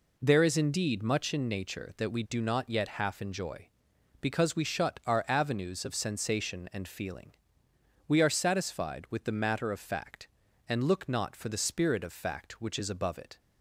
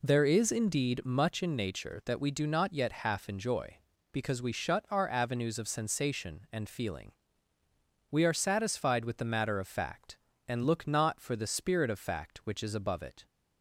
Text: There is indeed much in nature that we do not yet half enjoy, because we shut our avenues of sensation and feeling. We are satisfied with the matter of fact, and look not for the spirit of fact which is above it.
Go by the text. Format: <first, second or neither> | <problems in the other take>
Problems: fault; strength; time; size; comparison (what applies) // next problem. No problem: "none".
neither | none